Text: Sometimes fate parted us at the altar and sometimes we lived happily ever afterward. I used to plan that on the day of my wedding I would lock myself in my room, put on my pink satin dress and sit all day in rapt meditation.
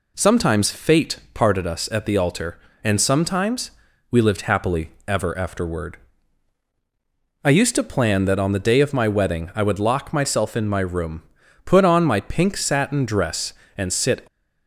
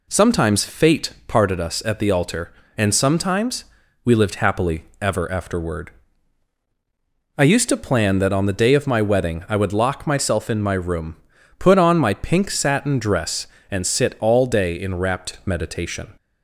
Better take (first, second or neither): second